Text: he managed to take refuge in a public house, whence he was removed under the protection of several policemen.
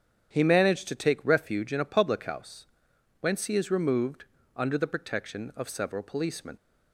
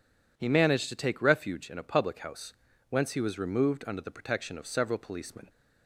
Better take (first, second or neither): second